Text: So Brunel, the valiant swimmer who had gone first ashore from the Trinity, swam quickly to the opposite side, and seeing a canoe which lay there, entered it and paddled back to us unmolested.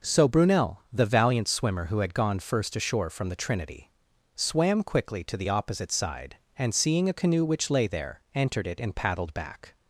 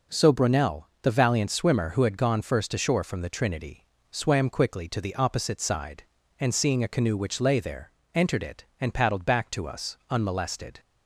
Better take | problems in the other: second | stops before "to us unmolested"; at 9.7 s

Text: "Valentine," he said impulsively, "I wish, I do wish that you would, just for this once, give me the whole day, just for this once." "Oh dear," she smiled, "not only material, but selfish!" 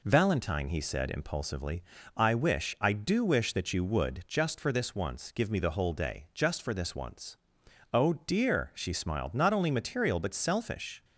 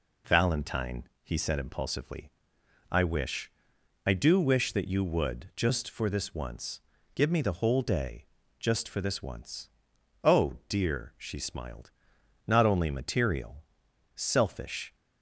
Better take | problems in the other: first | skips "but"; at 13.8 s

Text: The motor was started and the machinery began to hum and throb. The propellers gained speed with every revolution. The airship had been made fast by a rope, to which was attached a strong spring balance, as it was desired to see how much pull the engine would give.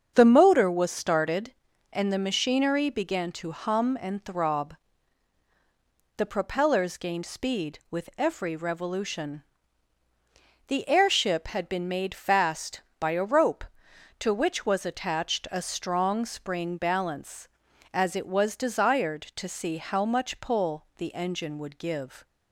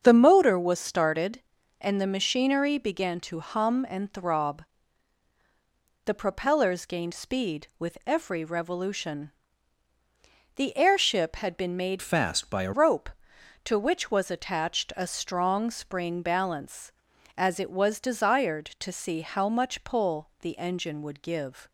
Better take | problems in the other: first | starts louder than the rest; until 1.0 s; 7 dB; also in the first // changes voice from "fast" to "a"; from 12.0 to 12.7 s; 0.7 s long

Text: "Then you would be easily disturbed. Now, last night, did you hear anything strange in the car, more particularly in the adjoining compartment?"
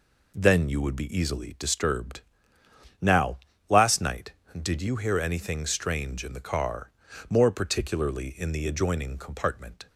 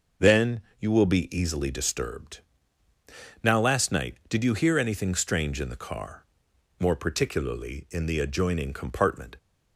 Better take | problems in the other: first | pauses between "Then" and "you"; slight; at 0.6 s; 0.18 s long // says "will" for "would"; at 0.9 s

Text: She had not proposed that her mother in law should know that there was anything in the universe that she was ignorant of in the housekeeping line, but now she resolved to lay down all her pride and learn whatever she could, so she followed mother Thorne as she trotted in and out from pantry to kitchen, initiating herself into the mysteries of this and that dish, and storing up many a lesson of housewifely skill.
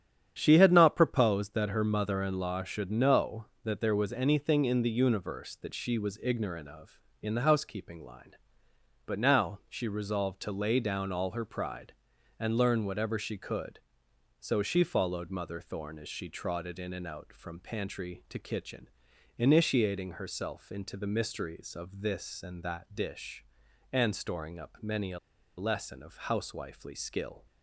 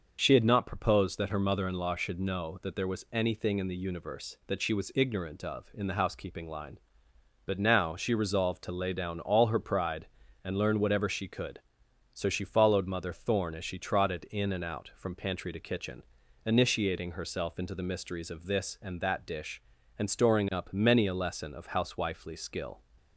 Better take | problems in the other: second | starts louder than the rest; strong; until 1.3 s; 9 dB; noticeable in the second // pauses between "a" and "lesson"; at 25.1 s; 0.39 s long

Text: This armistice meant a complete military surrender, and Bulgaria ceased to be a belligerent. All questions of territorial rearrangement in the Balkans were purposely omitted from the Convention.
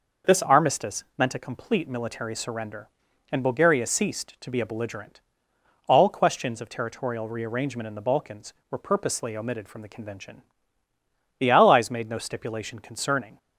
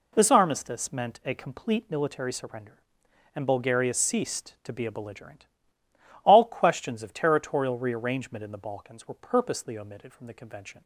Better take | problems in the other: second | goes on to say "The Allies made no stipulation concerning"; strong; from 11.3 s on; 2.0 s long

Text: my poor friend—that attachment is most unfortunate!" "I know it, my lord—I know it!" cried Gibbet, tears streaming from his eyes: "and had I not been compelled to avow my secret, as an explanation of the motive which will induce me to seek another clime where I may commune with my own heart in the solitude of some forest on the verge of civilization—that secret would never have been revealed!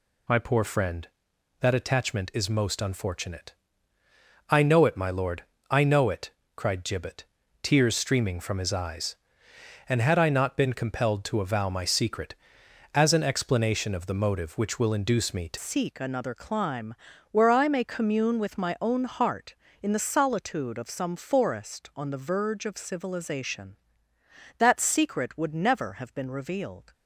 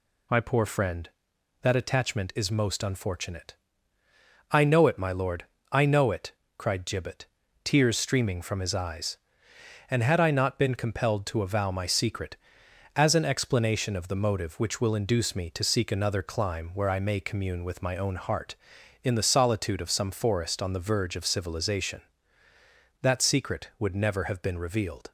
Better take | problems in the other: second | changes voice at "seek"; from 15.5 s on; 11.4 s long // pauses between "clime" and "where"; at 16.9 s; 0.38 s long

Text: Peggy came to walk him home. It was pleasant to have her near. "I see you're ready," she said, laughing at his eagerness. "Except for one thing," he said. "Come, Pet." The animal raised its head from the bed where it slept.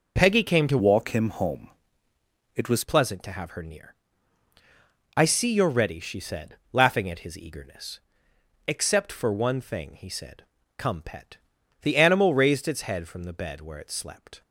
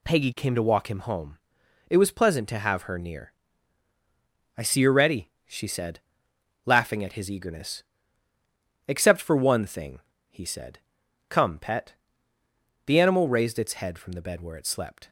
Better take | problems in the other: second | changes voice from "walk" to "was"; from 0.7 to 2.8 s; 2.1 s long

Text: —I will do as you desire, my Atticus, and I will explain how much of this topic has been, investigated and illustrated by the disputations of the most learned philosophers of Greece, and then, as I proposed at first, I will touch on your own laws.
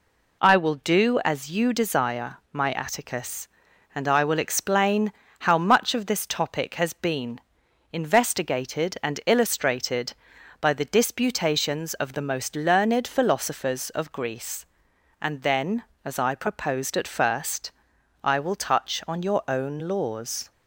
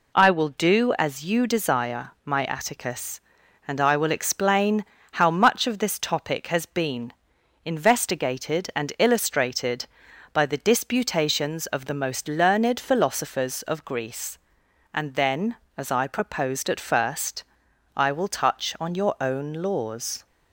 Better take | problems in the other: neither | pauses between "explain" and "how"; slight; the same in both

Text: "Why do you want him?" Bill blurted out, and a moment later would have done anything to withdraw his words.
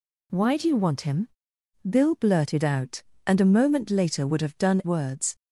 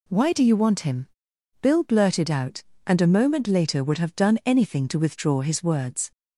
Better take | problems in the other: second | skips "anything to withdraw his"; at 4.8 s

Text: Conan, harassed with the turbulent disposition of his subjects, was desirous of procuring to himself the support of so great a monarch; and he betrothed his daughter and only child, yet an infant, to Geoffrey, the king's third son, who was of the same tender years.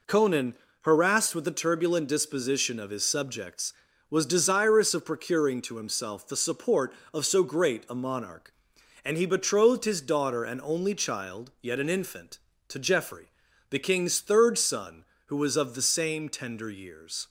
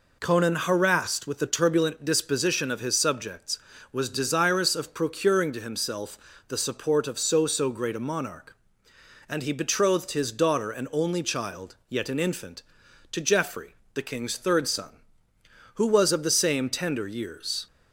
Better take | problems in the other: first | pauses between "himself" and "the"; slight; at 6.1 s; 0.30 s long // says "so" twice; at 7.4 s

